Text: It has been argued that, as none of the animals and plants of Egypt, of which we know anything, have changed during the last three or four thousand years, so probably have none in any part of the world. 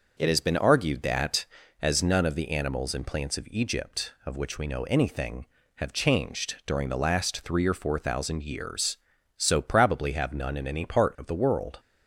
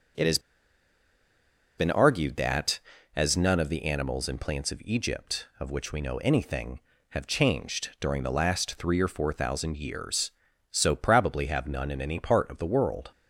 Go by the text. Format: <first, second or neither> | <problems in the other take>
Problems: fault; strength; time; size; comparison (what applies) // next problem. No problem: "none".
first | pauses between "has" and "been"; strong; at 0.3 s; 1.3 s long